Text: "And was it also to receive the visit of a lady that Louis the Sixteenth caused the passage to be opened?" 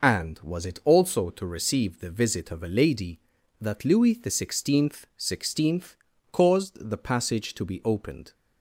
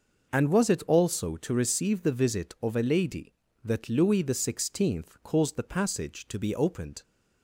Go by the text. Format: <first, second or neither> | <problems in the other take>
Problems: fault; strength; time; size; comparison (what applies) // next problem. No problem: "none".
second | says "Sixteenth" twice; at 5.1 s